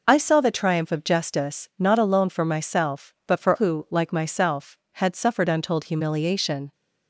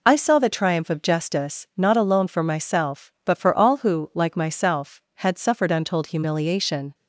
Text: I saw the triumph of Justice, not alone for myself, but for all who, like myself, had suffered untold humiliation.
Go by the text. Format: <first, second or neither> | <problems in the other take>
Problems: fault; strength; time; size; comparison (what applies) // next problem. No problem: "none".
second | skips "all"; at 3.5 s